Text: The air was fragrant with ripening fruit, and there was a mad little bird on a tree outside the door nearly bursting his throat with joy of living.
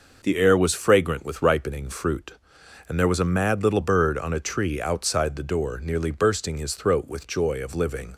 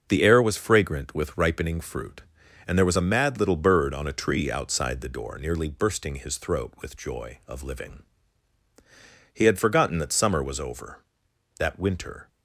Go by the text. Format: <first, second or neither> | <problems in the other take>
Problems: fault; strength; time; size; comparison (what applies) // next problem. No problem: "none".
first | starts louder than the rest; until 1.1 s; 6 dB // goes on to say "He had forgotten that summer was over that winter"; strong; from 9.3 s on; 2.9 s long